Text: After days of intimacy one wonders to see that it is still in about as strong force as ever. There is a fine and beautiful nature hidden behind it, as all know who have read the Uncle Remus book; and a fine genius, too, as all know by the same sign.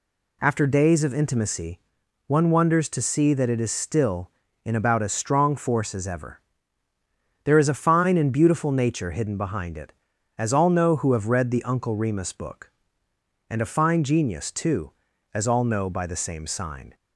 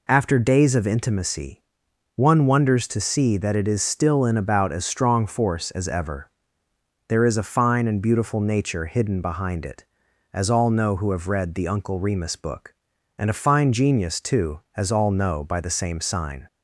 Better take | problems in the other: neither | pauses between "intimacy" and "one"; noticeable; the same in both

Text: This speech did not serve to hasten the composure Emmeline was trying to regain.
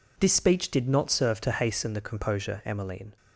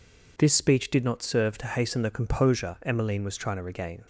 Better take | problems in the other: second | stops before "was trying to regain"; at 3.1 s

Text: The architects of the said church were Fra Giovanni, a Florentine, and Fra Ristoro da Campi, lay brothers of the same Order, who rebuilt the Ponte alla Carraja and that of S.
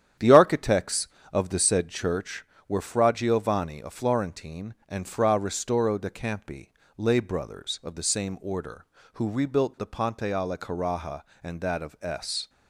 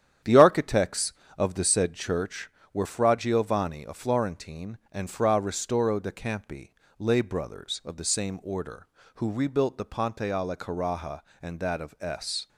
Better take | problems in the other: neither | starts louder than the rest; strong; the same in both

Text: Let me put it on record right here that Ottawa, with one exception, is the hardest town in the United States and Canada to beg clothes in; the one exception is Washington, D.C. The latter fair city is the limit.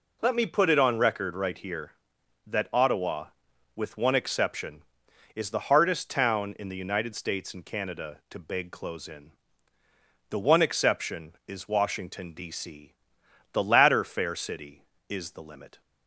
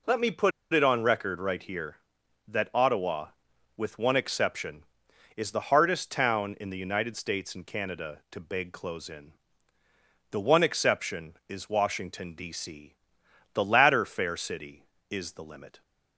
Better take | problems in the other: first | pauses between "put" and "it"; slight; at 0.5 s; 0.22 s long

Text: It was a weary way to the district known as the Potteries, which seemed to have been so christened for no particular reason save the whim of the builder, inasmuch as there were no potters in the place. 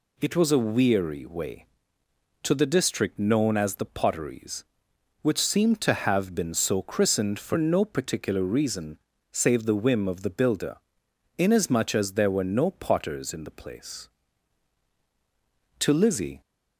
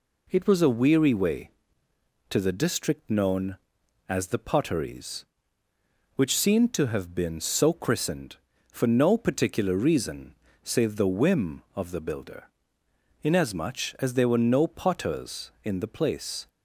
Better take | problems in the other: second | pauses between "reason" and "save"; slight; at 8.9 s; 0.34 s long; slight in the second // goes on to say "To Lizzie"; from 15.8 s on; 0.60 s long

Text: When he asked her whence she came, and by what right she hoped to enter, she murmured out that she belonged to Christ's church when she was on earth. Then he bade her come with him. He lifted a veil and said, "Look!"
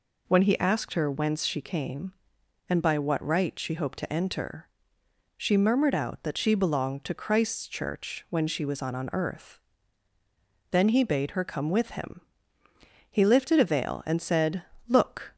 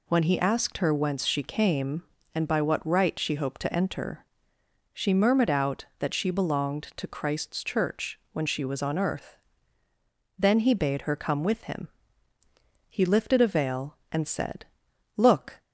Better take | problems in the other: second | says "on" twice; at 8.9 s

